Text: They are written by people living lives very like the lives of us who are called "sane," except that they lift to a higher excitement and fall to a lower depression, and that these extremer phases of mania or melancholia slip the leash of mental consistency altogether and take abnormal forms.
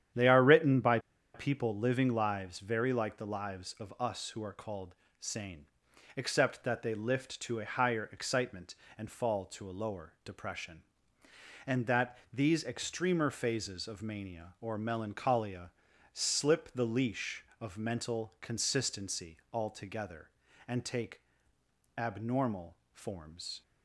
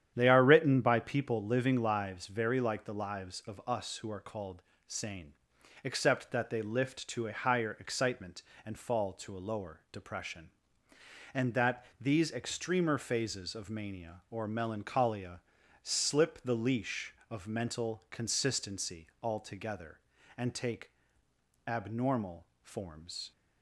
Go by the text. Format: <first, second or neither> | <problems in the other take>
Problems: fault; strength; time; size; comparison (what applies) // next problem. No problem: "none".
second | starts louder than the rest; strong; until 1.5 s; 10 dB; strong in the second // pauses between "by" and "people"; slight; at 0.9 s; 0.35 s long // pauses between "called" and "sane"; slight; at 4.9 s; 0.24 s long; slight in the second // pauses between "that" and "these"; slight; at 12.1 s; 0.16 s long; slight in the second // pauses between "melancholia" and "slip"; at 15.7 s; 0.42 s long; also in the second // pauses between "take" and "abnormal"; noticeable; at 21.2 s; 0.76 s long; noticeable in the second // pauses between "abnormal" and "forms"; slight; at 22.7 s; 0.16 s long; slight in the second